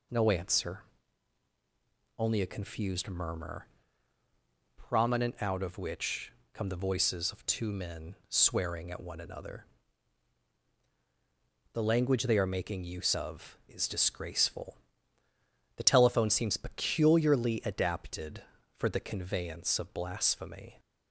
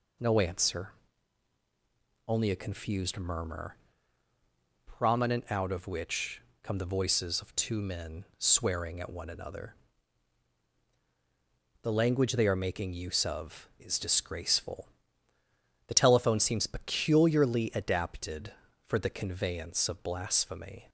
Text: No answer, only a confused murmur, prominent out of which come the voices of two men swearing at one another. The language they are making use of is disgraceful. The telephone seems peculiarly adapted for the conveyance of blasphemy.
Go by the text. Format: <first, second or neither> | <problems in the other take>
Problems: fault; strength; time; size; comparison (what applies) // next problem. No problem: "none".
neither | pauses between "which" and "come"; slight; the same in both